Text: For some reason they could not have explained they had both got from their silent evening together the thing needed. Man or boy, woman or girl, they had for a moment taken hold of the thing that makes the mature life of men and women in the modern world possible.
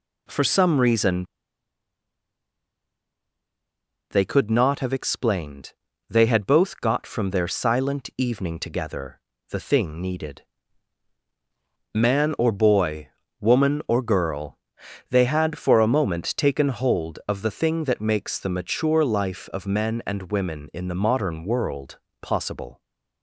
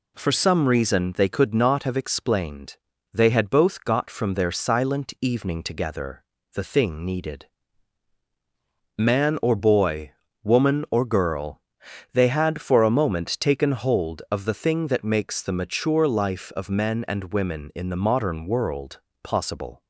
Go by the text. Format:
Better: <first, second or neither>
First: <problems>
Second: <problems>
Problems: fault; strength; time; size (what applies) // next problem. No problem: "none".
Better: second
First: pauses between "reason" and "they"; strong; at 1.2 s; 2.8 s long // pauses between "explained" and "they"; slight; at 5.7 s; 0.36 s long // pauses between "together" and "the"; slight; at 9.1 s; 0.30 s long // pauses between "world" and "possible"; slight; at 21.9 s; 0.24 s long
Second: pauses between "explained" and "they"; slight; at 2.7 s; 0.36 s long // pauses between "together" and "the"; slight; at 6.2 s; 0.30 s long // pauses between "world" and "possible"; slight; at 18.9 s; 0.24 s long